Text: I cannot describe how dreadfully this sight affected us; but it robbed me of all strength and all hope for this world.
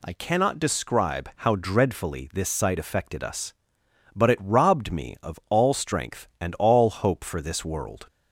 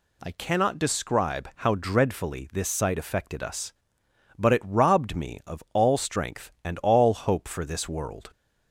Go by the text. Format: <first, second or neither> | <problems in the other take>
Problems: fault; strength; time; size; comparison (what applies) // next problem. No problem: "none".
neither | none